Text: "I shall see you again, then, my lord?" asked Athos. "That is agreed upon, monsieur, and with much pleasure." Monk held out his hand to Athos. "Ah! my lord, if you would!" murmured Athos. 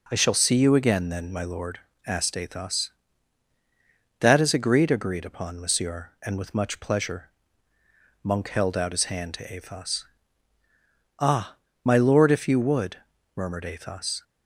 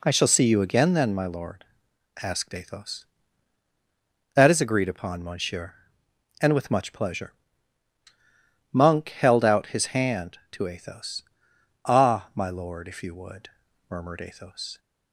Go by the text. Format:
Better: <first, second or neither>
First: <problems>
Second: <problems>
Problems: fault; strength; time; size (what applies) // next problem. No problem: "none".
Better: second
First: says "agreed" twice; at 4.8 s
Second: none